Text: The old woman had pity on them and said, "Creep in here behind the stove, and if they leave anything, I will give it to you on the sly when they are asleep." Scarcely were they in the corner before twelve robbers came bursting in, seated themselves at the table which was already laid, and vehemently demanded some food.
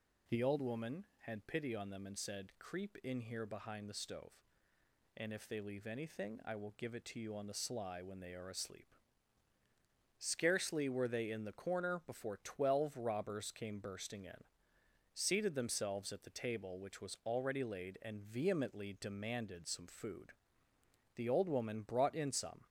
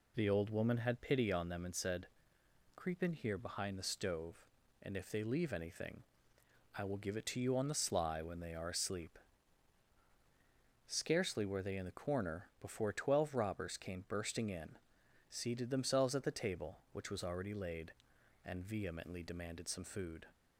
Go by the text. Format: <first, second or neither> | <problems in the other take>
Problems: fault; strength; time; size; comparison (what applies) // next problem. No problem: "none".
second | goes on to say "The old woman brought in some"; from 21.1 s on; 1.5 s long